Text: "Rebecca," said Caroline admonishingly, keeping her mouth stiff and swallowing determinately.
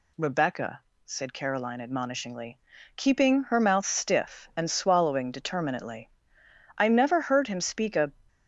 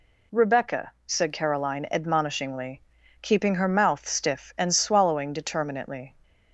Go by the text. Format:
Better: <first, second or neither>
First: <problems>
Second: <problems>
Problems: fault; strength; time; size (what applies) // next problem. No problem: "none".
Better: second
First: goes on to say "I never heard him speak a"; from 6.7 s on; 1.3 s long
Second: none